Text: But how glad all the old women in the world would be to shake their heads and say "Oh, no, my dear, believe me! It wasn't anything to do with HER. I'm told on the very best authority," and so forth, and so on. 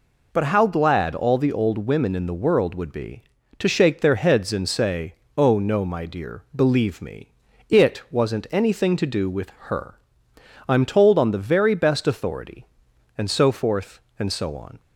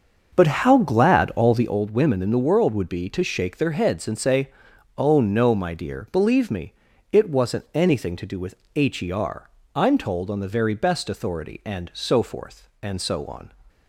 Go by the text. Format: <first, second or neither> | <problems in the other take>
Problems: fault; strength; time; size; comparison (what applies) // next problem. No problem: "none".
first | starts louder than the rest; until 1.8 s; 6.5 dB // pauses between "say" and "Oh"; noticeable; at 4.4 s; 0.48 s long; slight in the first // pauses between "with" and "HER"; slight; at 8.5 s; 0.20 s long; slight in the first